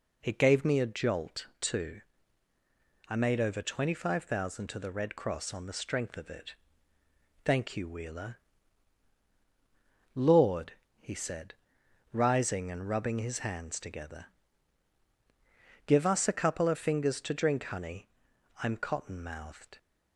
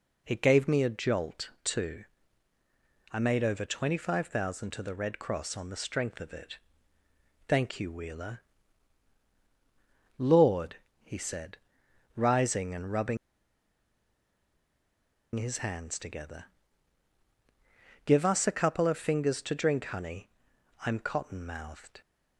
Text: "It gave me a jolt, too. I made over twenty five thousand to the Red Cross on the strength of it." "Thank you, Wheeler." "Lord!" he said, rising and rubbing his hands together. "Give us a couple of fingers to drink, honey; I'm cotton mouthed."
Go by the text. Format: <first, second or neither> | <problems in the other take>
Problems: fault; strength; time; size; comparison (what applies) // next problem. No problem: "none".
first | pauses between "rubbing" and "his"; strong; at 13.1 s; 2.1 s long